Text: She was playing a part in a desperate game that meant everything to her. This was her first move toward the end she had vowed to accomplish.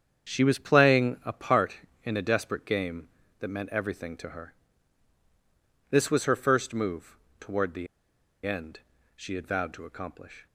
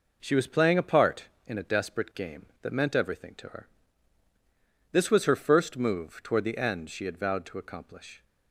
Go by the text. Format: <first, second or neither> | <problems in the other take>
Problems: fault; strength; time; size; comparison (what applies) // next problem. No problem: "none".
second | starts louder than the rest; strong; until 1.3 s; 8 dB // pauses between "move" and "toward"; slight; at 7.1 s; 0.22 s long // pauses between "the" and "end"; noticeable; at 7.8 s; 0.59 s long // pauses between "end" and "she"; slight; at 8.8 s; 0.36 s long